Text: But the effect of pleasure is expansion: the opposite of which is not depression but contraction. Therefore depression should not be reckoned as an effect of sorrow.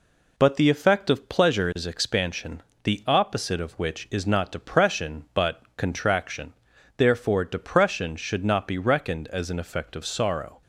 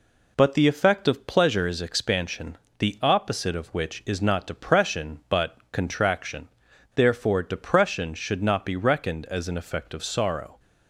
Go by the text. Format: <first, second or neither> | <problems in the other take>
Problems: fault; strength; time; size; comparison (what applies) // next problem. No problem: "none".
neither | none